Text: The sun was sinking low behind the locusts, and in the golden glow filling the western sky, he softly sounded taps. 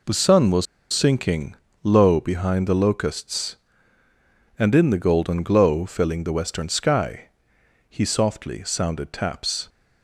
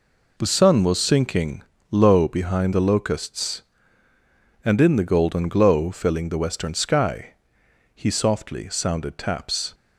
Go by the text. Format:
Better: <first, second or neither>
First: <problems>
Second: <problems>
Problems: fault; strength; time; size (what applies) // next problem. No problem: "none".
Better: second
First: pauses between "was" and "sinking"; slight; at 0.6 s; 0.27 s long // pauses between "sinking" and "low"; slight; at 1.5 s; 0.28 s long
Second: pauses between "sinking" and "low"; slight; at 1.6 s; 0.28 s long